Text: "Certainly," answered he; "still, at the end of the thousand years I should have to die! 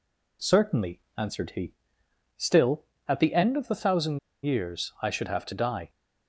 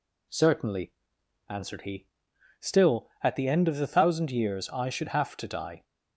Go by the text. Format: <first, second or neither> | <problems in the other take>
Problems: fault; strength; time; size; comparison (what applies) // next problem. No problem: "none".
second | pauses between "thousand" and "years"; slight; at 4.1 s; 0.26 s long